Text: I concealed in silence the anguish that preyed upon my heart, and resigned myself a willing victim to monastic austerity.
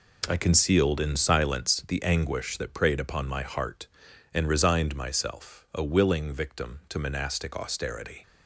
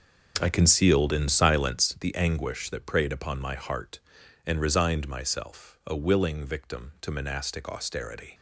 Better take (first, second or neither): first